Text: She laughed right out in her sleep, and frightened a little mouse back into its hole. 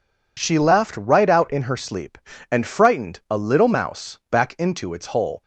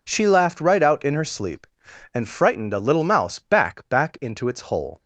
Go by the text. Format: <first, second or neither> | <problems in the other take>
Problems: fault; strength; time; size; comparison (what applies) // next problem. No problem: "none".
first | says "back" twice; at 3.8 s